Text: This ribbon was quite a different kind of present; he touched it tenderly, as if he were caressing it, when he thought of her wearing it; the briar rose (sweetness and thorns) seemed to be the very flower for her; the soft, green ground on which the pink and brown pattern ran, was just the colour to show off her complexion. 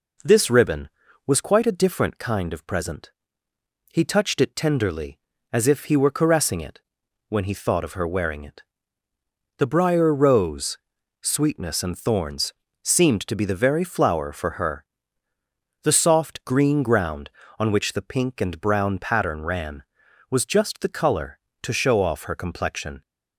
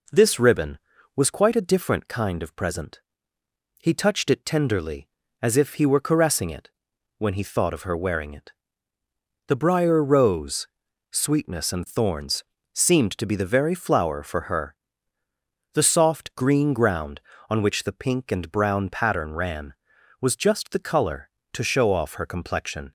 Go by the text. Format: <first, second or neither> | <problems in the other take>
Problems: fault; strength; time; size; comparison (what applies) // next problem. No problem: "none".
neither | none